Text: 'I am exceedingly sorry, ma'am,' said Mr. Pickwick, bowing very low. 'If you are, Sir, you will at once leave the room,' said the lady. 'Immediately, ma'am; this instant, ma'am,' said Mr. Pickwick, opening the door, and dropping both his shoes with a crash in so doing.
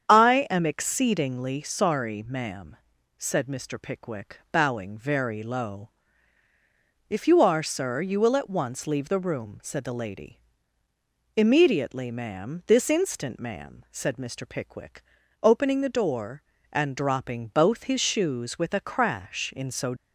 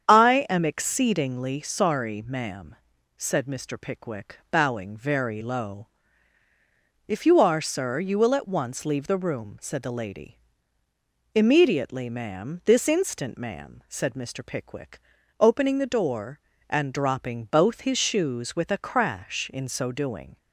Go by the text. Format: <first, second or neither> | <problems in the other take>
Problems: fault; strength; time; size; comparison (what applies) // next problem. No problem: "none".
second | starts louder than the rest; strong; until 1.1 s; 8 dB; strong in the second // stops before "doing"; at 19.9 s